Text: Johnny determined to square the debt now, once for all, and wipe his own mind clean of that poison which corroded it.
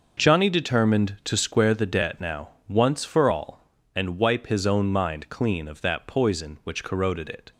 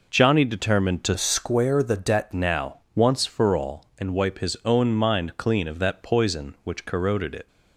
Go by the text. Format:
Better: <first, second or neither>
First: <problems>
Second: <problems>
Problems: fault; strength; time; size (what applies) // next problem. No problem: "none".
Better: first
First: none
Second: changes voice from "square" to "debt"; from 1.1 to 2.3 s; 1.2 s long